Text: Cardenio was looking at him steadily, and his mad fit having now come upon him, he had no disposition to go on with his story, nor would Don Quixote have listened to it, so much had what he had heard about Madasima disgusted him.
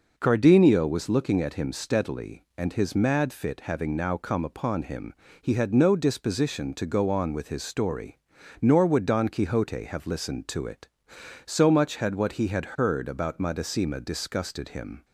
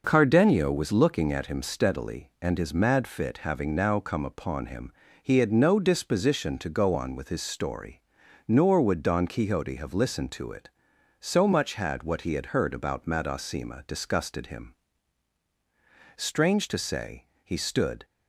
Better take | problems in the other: first | goes on to say "Strange to say he stood"; strong; from 16.1 s on; 1.8 s long

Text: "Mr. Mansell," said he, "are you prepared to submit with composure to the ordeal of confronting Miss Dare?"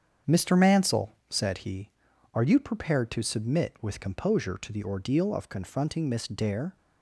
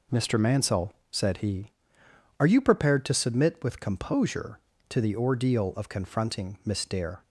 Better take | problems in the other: second | starts louder than the rest; strong; until 1.5 s; 7.5 dB

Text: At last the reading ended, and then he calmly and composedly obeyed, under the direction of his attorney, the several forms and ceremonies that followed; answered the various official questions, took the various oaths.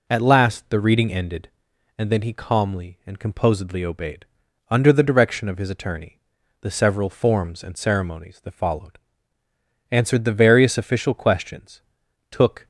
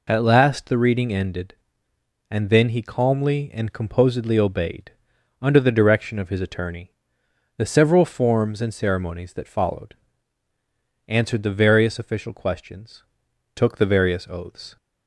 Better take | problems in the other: second | stops before "the various oaths"; at 12.6 s

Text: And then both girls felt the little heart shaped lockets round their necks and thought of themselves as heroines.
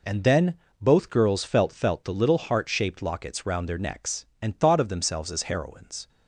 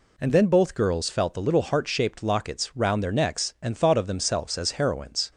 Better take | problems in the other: second | pauses between "then" and "both"; slight; at 0.5 s; 0.28 s long // says "felt" twice; at 1.7 s

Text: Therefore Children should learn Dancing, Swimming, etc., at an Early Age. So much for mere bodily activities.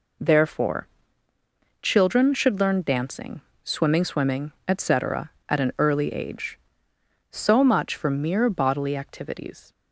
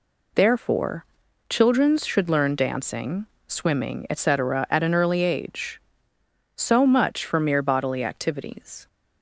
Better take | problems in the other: second | pauses between "Therefore" and "Children"; noticeable; at 0.8 s; 0.94 s long; also in the second // says "Swimming" twice; at 4.0 s

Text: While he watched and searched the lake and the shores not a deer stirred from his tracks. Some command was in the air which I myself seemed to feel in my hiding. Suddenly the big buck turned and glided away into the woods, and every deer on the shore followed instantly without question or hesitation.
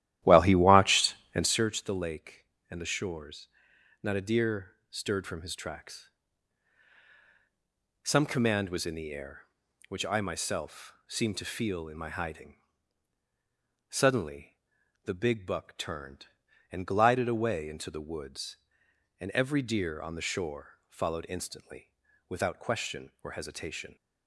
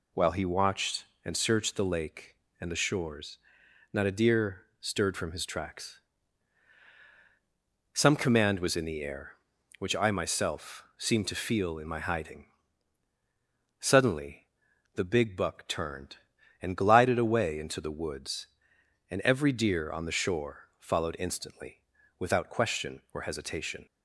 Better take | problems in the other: second | starts louder than the rest; strong; until 1.7 s; 13 dB // pauses between "shores" and "not"; noticeable; at 3.4 s; 0.52 s long; noticeable in the second // pauses between "deer" and "stirred"; slight; at 4.7 s; 0.16 s long; slight in the second // pauses between "Suddenly" and "the"; noticeable; at 14.5 s; 0.48 s long; noticeable in the second // pauses between "instantly" and "without"; at 21.9 s; 0.38 s long; also in the second

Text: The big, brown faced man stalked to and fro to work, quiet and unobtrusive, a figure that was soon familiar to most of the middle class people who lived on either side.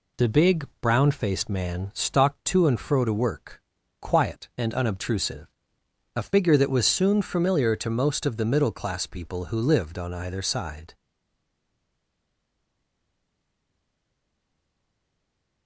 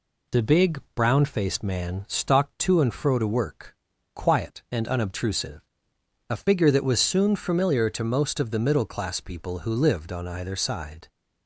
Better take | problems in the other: second | stays silent after the last word; strong; from 10.9 s on; 4.7 s long

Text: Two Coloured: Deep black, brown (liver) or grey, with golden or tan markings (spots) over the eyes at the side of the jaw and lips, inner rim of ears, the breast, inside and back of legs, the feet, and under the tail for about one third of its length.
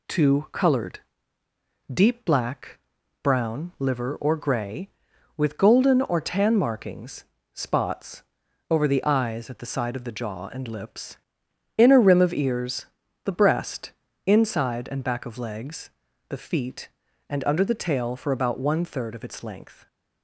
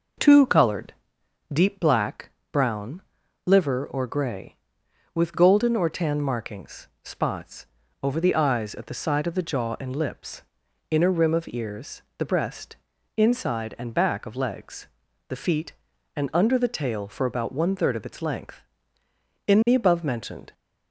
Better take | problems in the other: first | goes on to say "In the above mentioned"; noticeable; from 19.4 s on; 1.0 s long

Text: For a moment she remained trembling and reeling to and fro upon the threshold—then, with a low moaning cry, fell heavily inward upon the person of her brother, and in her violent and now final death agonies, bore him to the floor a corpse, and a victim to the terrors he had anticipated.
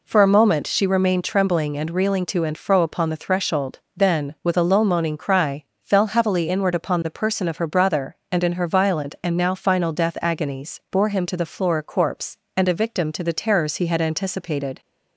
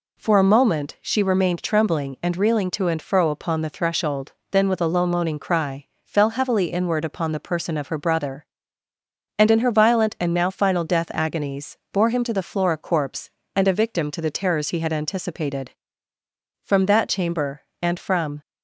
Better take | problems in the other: first | goes on to say "From that chamber and from"; strong; from 16.6 s on; 1.7 s long

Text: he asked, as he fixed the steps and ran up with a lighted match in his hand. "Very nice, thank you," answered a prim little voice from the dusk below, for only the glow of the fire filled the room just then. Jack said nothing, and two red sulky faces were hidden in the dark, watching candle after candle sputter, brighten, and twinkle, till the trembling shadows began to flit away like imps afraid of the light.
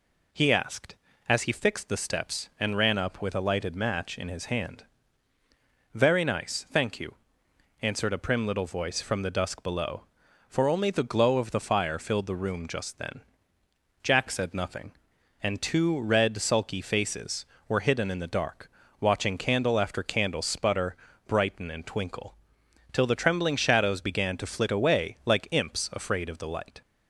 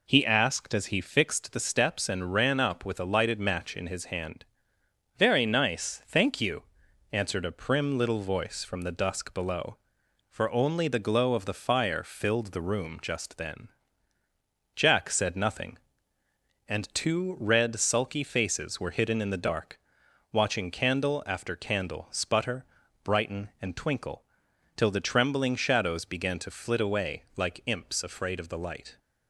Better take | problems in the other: neither | none

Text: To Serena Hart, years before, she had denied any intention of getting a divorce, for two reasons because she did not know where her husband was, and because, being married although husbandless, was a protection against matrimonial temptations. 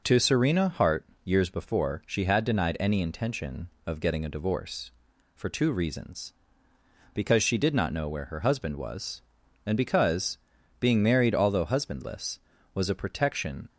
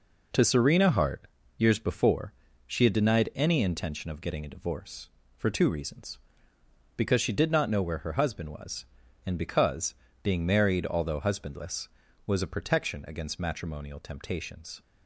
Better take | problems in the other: second | stops before "against matrimonial temptations"; at 13.6 s

